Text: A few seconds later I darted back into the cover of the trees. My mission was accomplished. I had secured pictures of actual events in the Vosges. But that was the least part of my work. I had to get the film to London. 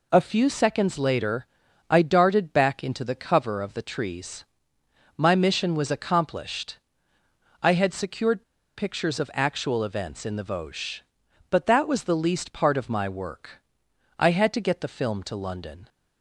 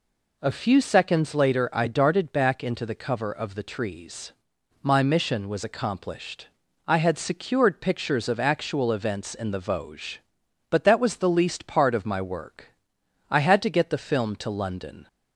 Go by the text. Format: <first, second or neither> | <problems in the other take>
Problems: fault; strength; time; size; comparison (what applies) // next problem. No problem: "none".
second | pauses between "later" and "I"; at 1.4 s; 0.42 s long // pauses between "secured" and "pictures"; at 8.4 s; 0.36 s long